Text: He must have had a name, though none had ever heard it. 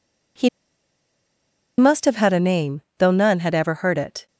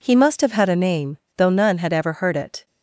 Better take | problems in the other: second | pauses between "He" and "must"; strong; at 0.4 s; 1.2 s long

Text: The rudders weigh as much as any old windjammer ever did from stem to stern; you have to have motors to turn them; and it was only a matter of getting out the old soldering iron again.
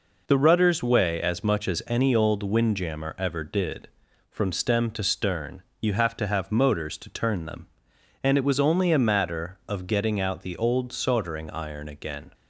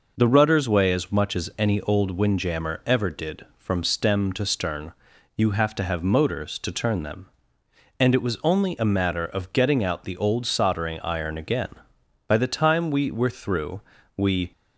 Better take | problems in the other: first | goes on to say "By the time we were through we"; strong; from 12.2 s on; 2.2 s long

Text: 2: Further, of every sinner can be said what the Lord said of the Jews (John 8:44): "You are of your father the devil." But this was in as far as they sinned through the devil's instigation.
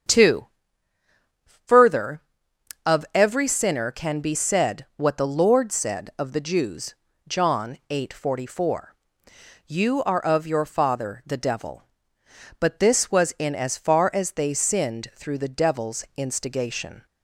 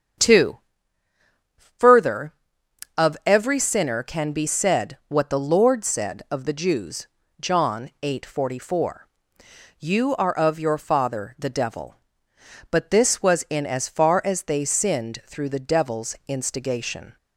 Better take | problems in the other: neither | starts louder than the rest; strong; the same in both

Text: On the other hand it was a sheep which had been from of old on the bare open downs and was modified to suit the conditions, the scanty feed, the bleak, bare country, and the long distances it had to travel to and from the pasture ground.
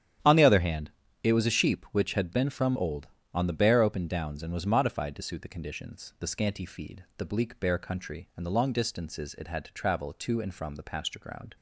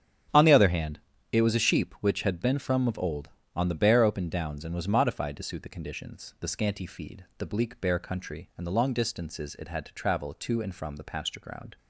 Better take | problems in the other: second | starts louder than the rest; strong; until 1.5 s; 10 dB; strong in the second // pauses between "hand" and "it"; slight; at 0.9 s; 0.32 s long; slight in the second // skips "of"; at 2.7 s

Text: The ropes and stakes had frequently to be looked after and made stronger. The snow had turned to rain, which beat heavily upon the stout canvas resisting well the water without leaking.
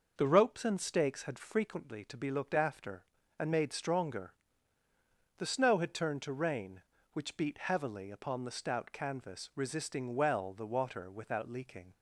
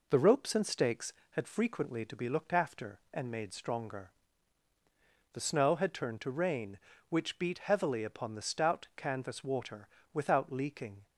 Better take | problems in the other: first | skips "resisting well the"; at 9.4 s // pauses between "water" and "without"; slight; at 9.8 s; 0.26 s long

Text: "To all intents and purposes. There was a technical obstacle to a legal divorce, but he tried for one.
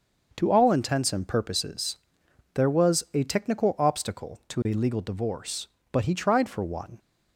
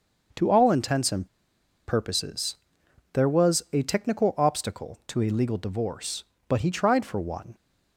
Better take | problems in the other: first | starts louder than the rest; until 1.9 s; 6.5 dB; also in the first // pauses between "and" and "purposes"; noticeable; at 1.2 s; 0.60 s long

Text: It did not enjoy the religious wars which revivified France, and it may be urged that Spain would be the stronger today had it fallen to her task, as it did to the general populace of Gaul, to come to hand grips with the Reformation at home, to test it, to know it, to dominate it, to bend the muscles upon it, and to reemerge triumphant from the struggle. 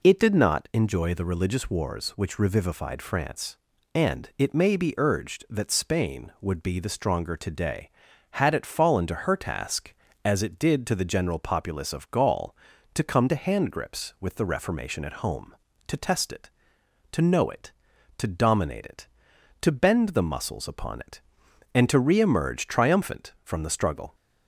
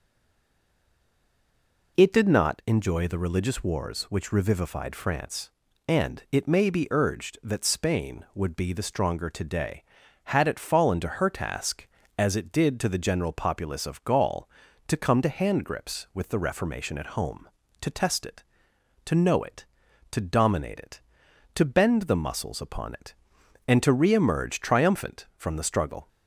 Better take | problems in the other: first | stays silent before the first word; noticeable; until 1.9 s; 1.9 s long

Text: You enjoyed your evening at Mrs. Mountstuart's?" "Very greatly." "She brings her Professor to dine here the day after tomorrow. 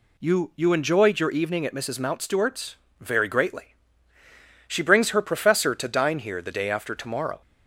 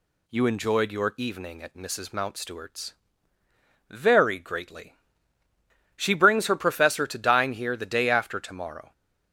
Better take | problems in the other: second | says "You" twice; at 0.5 s

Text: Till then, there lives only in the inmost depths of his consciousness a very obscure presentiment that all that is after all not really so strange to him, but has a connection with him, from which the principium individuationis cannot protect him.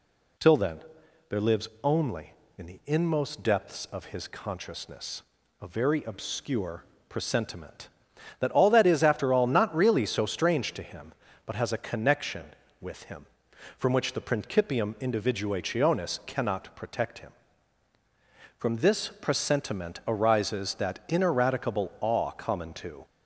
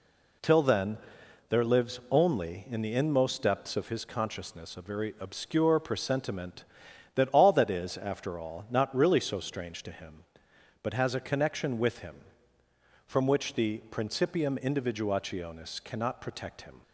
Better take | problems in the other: second | pauses between "consciousness" and "a"; at 5.2 s; 0.38 s long // pauses between "obscure" and "presentiment"; slight; at 6.8 s; 0.24 s long // goes on to say "From this presentiment arises that ineradicable awe common to"; strong; from 18.5 s on; 4.4 s long

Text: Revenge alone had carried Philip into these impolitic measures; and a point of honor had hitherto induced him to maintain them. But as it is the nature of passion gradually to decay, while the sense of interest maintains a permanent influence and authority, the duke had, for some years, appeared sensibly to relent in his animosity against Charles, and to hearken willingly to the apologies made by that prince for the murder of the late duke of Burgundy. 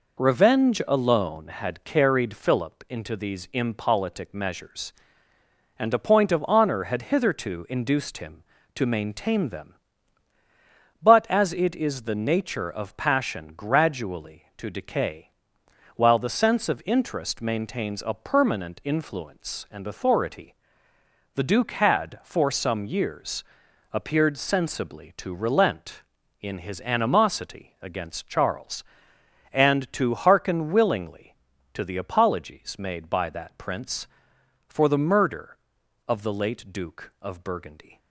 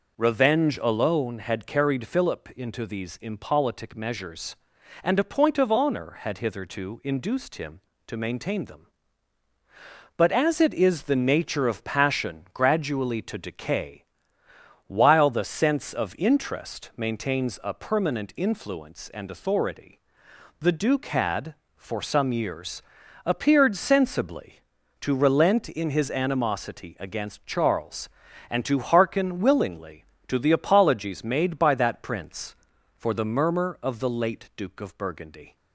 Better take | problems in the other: first | says "murmur" for "murder"; at 33.2 s

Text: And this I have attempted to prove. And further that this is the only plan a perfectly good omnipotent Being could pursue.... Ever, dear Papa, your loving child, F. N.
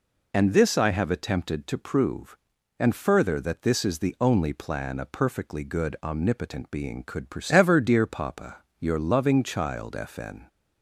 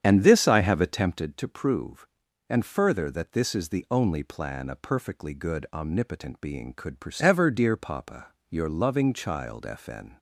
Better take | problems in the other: first | starts louder than the rest; strong; until 1.3 s; 8.5 dB

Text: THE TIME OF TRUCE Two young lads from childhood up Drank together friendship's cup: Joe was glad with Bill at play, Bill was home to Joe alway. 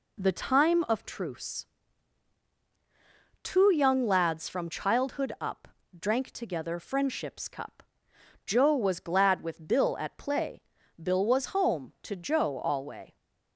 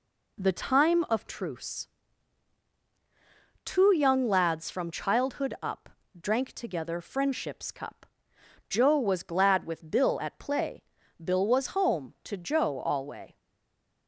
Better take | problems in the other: first | pauses between "TRUCE" and "Two"; strong; at 1.8 s; 1.7 s long; strong in the first // pauses between "up" and "Drank"; slight; at 5.8 s; 0.28 s long; slight in the first // stays silent after the last word; slight; from 13.3 s on; 0.7 s long

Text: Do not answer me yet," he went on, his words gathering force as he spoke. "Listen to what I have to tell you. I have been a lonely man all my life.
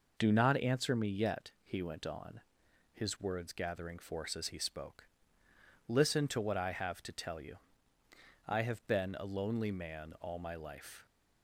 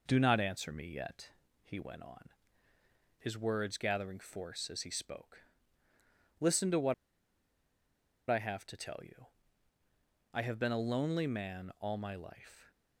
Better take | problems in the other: first | pauses between "what" and "I"; strong; at 6.9 s; 1.3 s long

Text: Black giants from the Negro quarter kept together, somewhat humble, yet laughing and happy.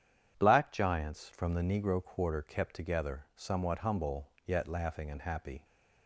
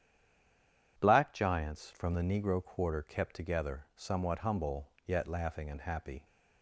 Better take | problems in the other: first | stays silent before the first word; slight; until 0.9 s; 0.9 s long

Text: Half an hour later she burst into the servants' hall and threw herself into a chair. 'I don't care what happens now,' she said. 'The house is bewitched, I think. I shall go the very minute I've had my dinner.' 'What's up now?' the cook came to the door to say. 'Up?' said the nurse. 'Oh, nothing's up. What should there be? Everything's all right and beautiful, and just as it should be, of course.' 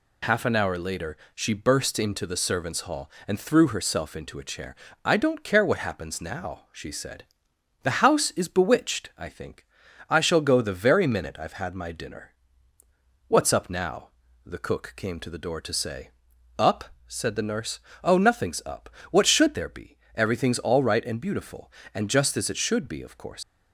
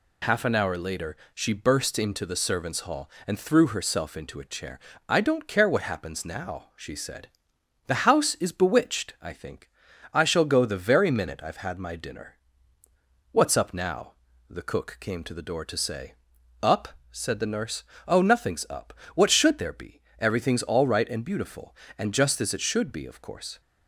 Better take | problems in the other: second | pauses between "later" and "she"; slight; at 1.1 s; 0.18 s long; slight in the second // leaves "course" unfinished; at 23.4 s; 135 ms

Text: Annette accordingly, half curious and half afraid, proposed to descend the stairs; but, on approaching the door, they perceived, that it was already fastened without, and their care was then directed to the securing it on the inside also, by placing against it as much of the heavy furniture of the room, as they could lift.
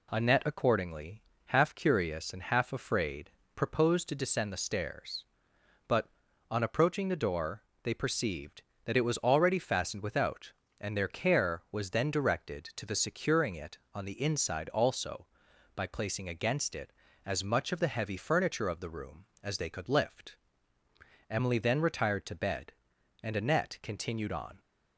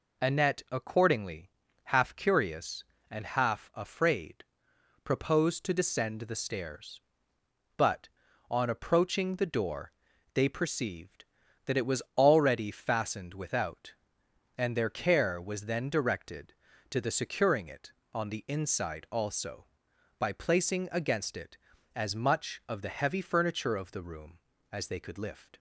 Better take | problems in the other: second | goes on to say "Emily then retired to bed and Annette continued on"; strong; from 21.2 s on; 3.3 s long

